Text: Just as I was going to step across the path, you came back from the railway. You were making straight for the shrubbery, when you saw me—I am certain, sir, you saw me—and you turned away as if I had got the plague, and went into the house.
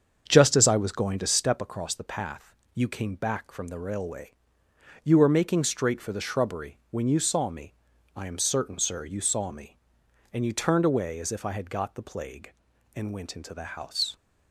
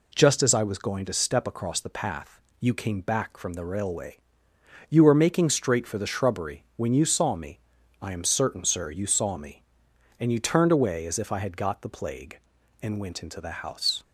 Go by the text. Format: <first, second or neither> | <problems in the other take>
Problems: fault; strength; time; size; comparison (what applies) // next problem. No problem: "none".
second | starts louder than the rest; strong; until 1.6 s; 7 dB